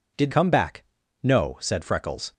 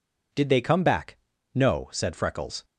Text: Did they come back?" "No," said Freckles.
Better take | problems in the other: second | skips "they"; at 0.3 s

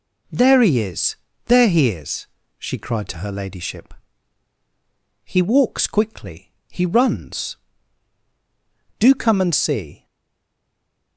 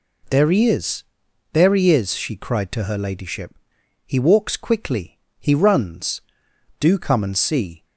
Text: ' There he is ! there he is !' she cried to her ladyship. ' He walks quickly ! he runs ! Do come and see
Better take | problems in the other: second | stays silent after the last word; noticeable; from 10.0 s on; 1.1 s long

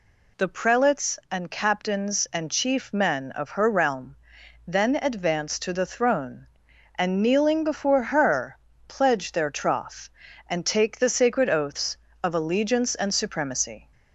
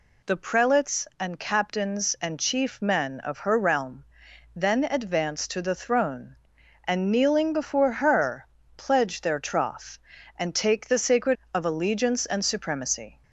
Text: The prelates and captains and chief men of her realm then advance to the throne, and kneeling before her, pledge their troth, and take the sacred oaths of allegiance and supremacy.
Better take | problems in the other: first | pauses between "realm" and "then"; noticeable; at 4.0 s; 0.50 s long; noticeable in the first // skips "oaths"; at 11.4 s

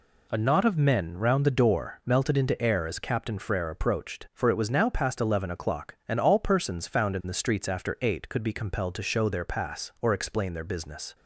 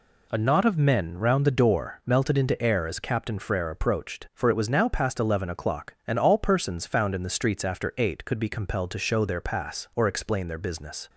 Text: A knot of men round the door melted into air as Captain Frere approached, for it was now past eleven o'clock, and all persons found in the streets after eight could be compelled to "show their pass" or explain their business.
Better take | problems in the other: neither | none

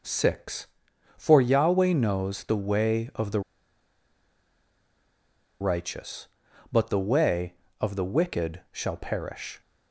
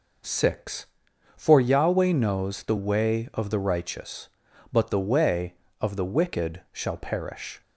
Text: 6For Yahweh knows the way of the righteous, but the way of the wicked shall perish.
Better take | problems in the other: second | pauses between "the" and "righteous"; strong; at 3.4 s; 2.2 s long

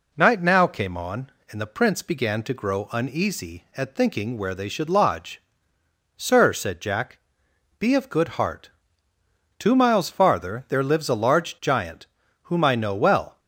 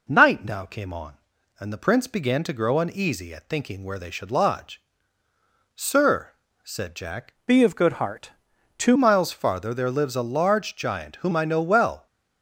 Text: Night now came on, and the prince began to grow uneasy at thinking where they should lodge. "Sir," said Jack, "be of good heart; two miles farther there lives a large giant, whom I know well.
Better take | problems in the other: first | changes voice from "be" to "two"; from 7.4 to 8.9 s; 1.5 s long

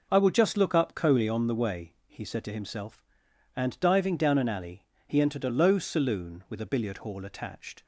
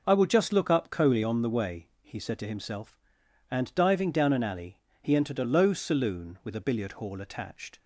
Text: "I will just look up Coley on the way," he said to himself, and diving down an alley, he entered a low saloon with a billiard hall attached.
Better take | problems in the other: neither | none

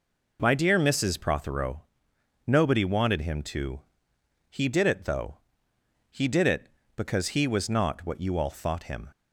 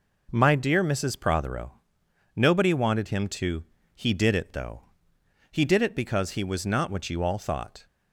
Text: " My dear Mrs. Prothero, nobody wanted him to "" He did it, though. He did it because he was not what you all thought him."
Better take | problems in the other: first | stops before "him"; at 7.8 s

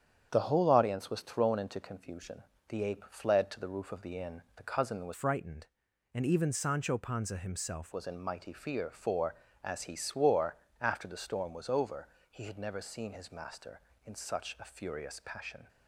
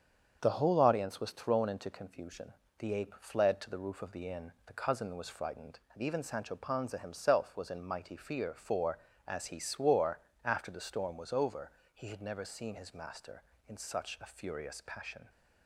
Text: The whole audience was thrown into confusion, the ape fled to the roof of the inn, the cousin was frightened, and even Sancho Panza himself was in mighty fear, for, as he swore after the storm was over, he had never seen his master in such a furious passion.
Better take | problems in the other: second | starts louder than the rest; strong; until 1.3 s; 8.5 dB; strong in the second // changes voice from "frightened" to "himself"; from 5.1 to 7.9 s; 2.8 s long // pauses between "swore" and "after"; slight; at 10.5 s; 0.26 s long; slight in the second

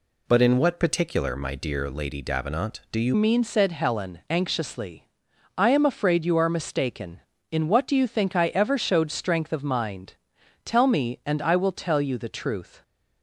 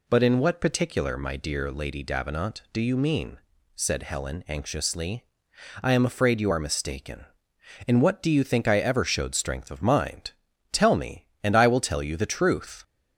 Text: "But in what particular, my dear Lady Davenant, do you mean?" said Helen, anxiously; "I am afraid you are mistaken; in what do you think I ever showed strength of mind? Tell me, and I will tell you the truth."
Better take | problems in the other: second | changes voice at "mean"; from 3.1 s on; 9.7 s long

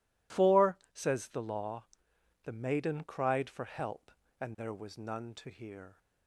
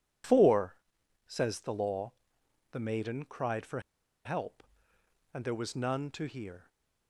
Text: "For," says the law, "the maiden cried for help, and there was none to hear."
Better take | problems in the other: first | pauses between "for" and "help"; at 3.8 s; 0.43 s long

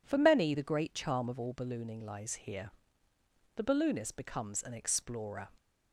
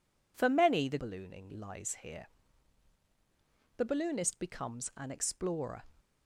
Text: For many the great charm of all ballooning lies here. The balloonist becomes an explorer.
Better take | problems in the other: first | skips "great charm of all"; at 0.9 s

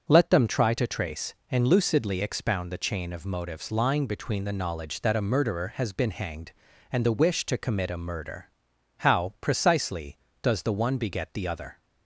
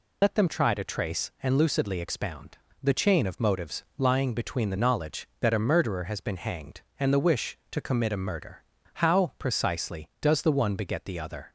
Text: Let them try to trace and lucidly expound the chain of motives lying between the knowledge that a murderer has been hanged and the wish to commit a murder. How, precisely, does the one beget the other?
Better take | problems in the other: first | loses the start of "Let"; at 0.2 s; 90 ms // pauses between "expound" and "the"; slight; at 2.5 s; 0.26 s long

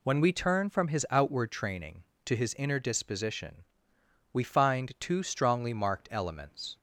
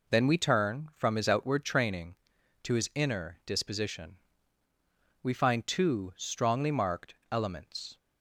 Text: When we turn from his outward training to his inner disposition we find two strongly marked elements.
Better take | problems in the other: first | says "Then" for "When"; at 0.0 s // pauses between "disposition" and "we"; at 4.1 s; 1.0 s long; noticeable in the first

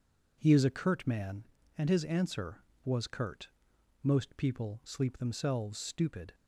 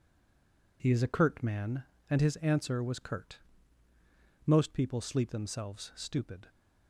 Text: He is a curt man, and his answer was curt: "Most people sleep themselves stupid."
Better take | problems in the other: first | stays silent before the first word; slight; until 0.7 s; 0.7 s long

